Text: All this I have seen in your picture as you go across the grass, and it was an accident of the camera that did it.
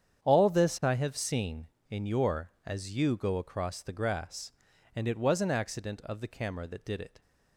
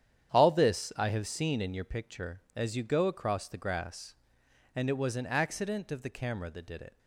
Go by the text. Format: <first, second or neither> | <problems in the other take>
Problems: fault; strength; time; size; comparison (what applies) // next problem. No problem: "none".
second | starts louder than the rest; strong; until 1.2 s; 8.5 dB; strong in the second // skips "picture"; at 2.5 s